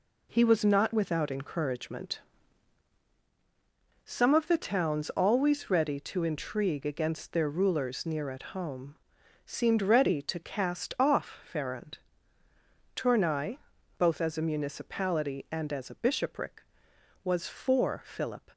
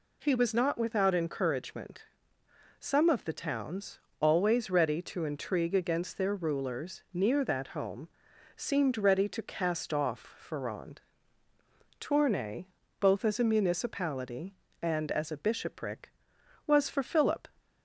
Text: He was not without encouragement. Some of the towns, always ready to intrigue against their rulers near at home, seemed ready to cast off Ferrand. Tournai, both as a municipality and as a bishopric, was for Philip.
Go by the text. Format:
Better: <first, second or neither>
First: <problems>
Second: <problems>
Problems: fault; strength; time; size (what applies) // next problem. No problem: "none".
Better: first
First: none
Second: says "that" for "at"; at 7.4 s